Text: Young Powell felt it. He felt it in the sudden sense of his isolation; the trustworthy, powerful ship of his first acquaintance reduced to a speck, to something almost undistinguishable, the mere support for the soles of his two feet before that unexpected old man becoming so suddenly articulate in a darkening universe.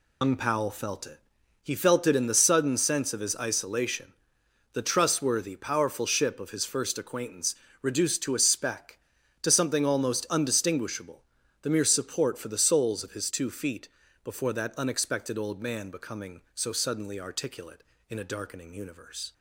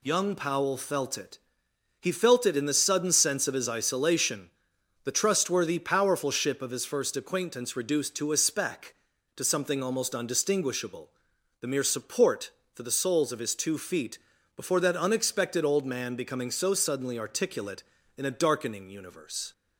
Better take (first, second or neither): second